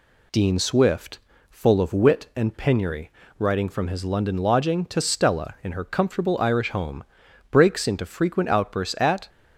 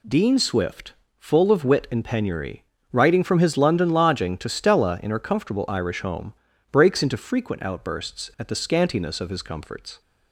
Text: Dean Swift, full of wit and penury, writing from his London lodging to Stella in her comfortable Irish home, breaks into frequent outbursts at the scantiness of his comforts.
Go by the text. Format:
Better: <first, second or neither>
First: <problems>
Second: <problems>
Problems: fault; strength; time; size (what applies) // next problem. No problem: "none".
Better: second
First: stops before "the scantiness of his comforts"; at 9.2 s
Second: none